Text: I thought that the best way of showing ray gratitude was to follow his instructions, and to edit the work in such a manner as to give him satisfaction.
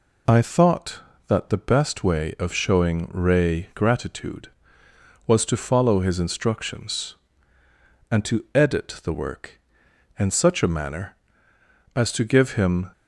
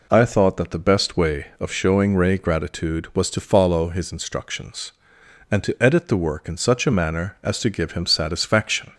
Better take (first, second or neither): second